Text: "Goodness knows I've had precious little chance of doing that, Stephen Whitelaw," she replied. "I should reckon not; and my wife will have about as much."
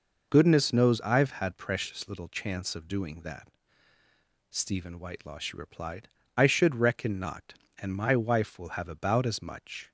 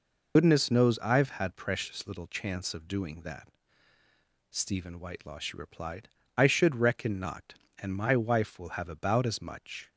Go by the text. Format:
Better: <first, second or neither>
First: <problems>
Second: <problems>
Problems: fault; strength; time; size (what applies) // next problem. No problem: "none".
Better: first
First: none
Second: loses the start of "Goodness"; at 0.3 s; 75 ms